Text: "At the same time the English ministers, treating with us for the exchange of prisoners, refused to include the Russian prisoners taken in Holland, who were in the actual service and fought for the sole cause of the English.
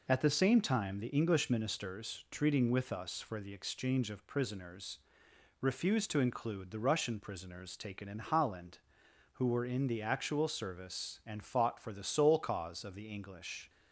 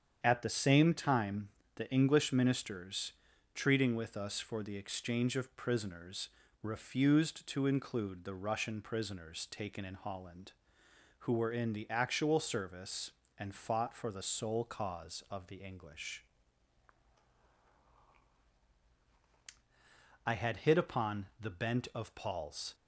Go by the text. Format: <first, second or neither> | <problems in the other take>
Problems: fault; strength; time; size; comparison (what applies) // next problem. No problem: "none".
first | starts louder than the rest; strong; until 1.2 s; 8 dB // pauses between "time" and "the"; slight; at 1.4 s; 0.26 s long // goes on to say "I had hit upon the bent of Paul's"; strong; from 20.2 s on; 2.5 s long